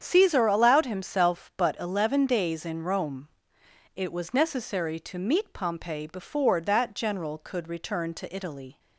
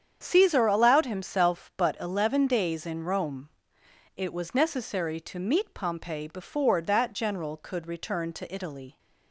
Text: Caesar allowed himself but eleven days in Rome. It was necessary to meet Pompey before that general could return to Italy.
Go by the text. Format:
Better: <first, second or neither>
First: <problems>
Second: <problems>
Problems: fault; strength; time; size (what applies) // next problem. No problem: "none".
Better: neither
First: starts louder than the rest; strong; until 1.0 s; 8 dB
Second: starts louder than the rest; strong; until 1.2 s; 8 dB